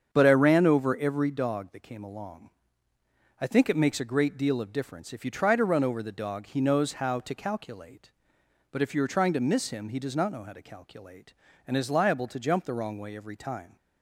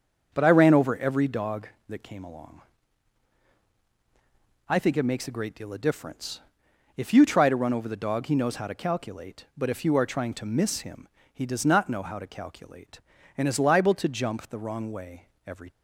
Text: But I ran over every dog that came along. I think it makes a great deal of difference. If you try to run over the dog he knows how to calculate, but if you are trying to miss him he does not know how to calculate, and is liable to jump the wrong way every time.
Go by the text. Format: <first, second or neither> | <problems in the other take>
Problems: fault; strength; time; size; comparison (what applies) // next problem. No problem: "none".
first | starts louder than the rest; until 1.3 s; 6.5 dB; strong in the first // pauses between "him" and "he"; slight; at 11.0 s; 0.26 s long // pauses between "way" and "every"; slight; at 15.2 s; 0.18 s long // stops before "time"; at 15.6 s